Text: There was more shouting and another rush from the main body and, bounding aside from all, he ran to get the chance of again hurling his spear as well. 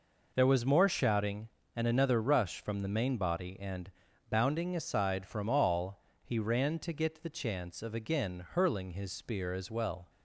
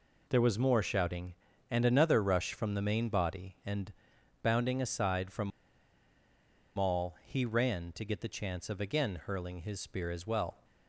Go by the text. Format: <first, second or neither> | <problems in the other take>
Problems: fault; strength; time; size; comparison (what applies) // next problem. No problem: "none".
first | pauses between "from" and "all"; strong; at 5.5 s; 1.2 s long